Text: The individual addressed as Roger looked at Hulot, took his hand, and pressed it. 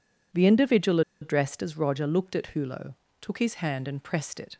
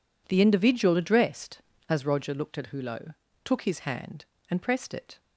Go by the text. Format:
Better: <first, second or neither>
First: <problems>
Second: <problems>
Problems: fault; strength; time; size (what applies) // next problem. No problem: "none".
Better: second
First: pauses between "individual" and "addressed"; slight; at 1.0 s; 0.20 s long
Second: none